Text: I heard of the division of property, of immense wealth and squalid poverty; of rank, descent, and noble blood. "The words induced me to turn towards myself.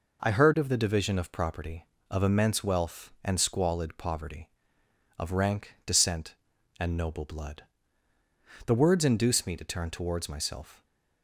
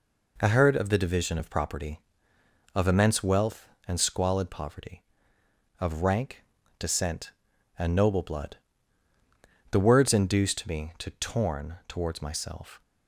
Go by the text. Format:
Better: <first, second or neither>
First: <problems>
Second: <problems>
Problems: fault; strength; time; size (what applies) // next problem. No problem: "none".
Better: first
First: none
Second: says "torn" for "turn"; at 11.1 s